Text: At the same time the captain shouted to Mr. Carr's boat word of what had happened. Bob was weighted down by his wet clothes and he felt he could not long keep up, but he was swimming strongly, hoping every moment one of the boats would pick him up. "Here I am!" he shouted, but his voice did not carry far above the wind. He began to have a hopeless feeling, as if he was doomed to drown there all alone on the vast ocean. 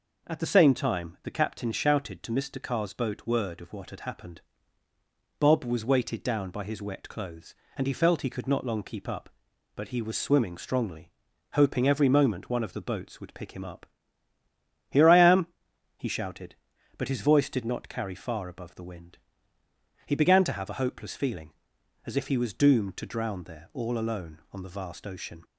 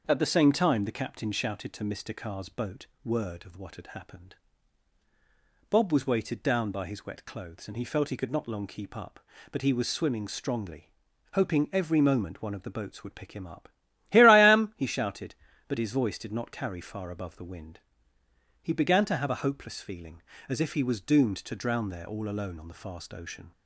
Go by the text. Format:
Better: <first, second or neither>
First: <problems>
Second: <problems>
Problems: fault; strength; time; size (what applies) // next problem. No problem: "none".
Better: first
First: none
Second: starts louder than the rest; until 1.0 s; 6 dB // pauses between "boat" and "word"; slight; at 2.8 s; 0.18 s long // says "fast" for "vast"; at 22.8 s